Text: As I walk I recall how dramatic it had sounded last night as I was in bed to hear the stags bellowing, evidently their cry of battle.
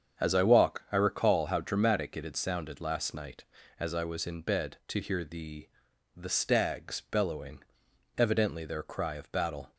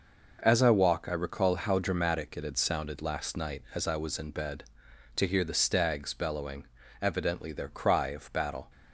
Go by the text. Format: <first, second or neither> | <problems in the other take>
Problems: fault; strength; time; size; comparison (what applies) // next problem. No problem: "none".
second | starts louder than the rest; strong; until 1.2 s; 7.5 dB // says "the" twice; at 6.1 s